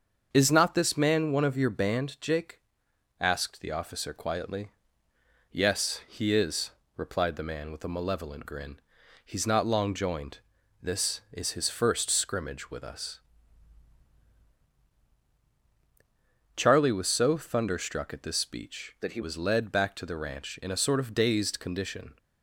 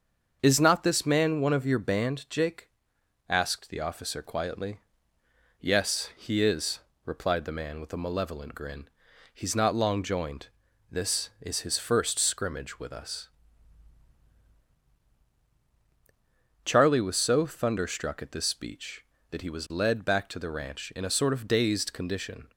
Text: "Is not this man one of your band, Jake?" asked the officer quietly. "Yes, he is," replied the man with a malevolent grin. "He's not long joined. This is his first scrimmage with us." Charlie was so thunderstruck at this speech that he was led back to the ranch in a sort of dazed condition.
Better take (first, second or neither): second